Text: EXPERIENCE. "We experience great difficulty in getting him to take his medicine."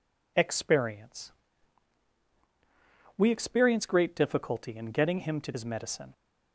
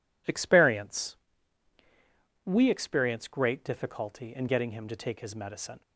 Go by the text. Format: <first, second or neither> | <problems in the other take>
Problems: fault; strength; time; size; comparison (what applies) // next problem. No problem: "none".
second | skips "take"; at 5.5 s